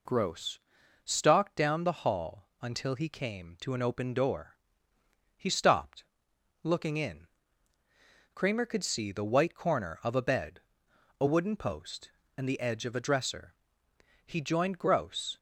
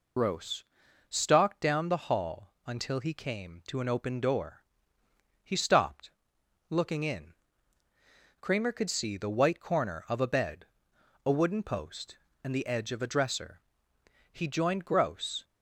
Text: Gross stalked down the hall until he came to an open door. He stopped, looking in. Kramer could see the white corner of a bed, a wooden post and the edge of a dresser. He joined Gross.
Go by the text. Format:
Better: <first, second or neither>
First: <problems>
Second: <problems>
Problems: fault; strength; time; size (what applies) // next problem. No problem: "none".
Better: first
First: pauses between "Gross" and "stalked"; at 0.6 s; 0.42 s long // pauses between "hall" and "until"; slight; at 2.4 s; 0.16 s long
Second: loses the start of "Gross"; at 0.1 s; 55 ms // pauses between "Gross" and "stalked"; at 0.6 s; 0.42 s long // pauses between "hall" and "until"; slight; at 2.5 s; 0.16 s long